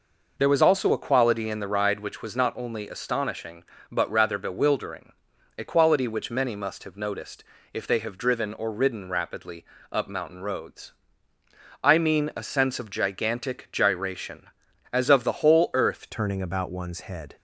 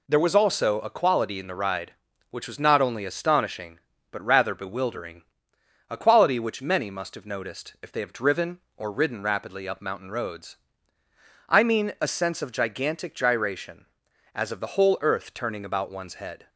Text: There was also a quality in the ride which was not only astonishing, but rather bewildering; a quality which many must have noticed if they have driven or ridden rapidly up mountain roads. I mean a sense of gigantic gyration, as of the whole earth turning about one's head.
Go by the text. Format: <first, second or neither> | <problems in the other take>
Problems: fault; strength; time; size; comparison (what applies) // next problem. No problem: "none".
second | pauses between "noticed" and "if"; slight; at 7.4 s; 0.30 s long // pauses between "rapidly" and "up"; slight; at 9.6 s; 0.26 s long // changes voice at "turning"; from 16.1 s on; 1.2 s long